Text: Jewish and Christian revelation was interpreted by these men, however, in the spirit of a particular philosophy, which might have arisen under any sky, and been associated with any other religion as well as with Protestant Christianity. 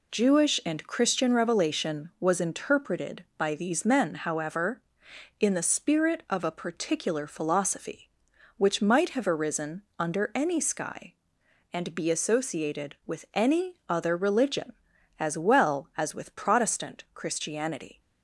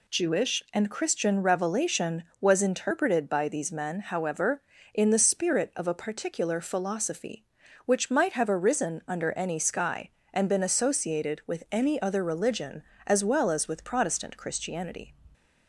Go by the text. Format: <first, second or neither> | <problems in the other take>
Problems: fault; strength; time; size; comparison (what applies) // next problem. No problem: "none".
second | pauses between "arisen" and "under"; slight; at 9.8 s; 0.16 s long // says "be" for "been"; at 11.9 s